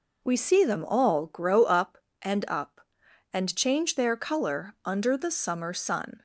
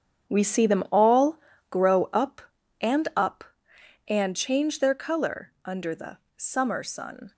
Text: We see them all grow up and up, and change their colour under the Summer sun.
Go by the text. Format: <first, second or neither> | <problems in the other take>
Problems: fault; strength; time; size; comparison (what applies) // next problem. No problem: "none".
first | gets quieter; strong; throughout; 13 dB // pauses between "all" and "grow"; slight; at 1.3 s; 0.32 s long // pauses between "the" and "Summer"; slight; at 6.1 s; 0.18 s long